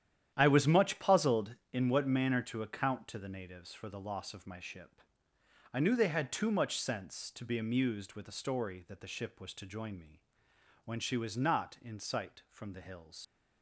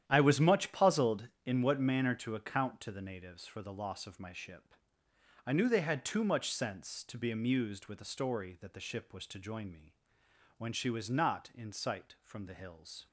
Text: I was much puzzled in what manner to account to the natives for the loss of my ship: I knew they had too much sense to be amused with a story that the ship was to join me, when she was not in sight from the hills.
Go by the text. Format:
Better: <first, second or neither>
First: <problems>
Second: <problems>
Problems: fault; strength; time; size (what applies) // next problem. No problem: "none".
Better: second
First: starts louder than the rest; strong; until 1.3 s; 10.5 dB // leaves "hills" unfinished; at 13.2 s; 95 ms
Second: starts louder than the rest; strong; until 1.0 s; 10.5 dB